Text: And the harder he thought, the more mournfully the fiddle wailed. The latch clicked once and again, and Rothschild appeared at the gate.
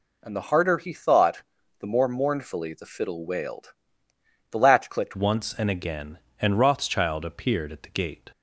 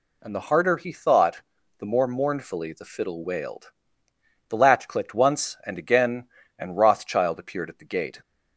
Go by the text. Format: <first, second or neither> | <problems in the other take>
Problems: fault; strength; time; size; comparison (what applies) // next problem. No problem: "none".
second | changes voice at "once"; from 5.1 s on; 3.2 s long